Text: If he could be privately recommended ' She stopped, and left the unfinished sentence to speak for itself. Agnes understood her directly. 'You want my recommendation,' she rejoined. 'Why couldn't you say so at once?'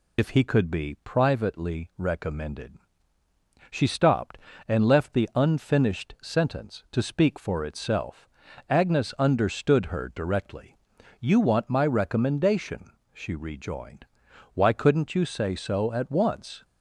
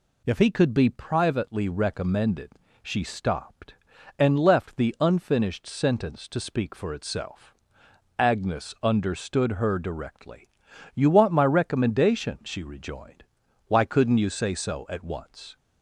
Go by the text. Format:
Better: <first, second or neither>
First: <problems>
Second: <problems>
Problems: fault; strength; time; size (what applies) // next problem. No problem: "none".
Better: second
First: loses the start of "If"; at 0.1 s; 60 ms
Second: none